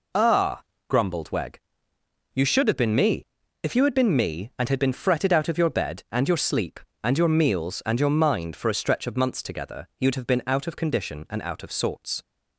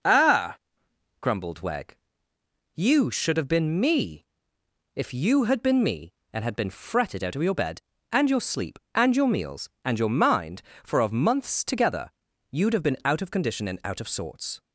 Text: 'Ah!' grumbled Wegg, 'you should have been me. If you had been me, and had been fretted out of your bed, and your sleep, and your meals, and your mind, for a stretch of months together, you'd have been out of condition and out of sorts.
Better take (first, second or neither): first